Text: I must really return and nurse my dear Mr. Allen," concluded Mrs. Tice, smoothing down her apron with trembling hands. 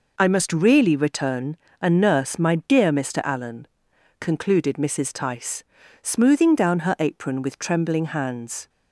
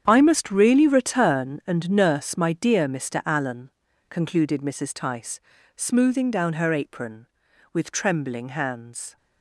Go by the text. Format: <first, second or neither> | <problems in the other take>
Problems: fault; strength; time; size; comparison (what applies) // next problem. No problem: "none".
first | gets quieter; strong; throughout; 13 dB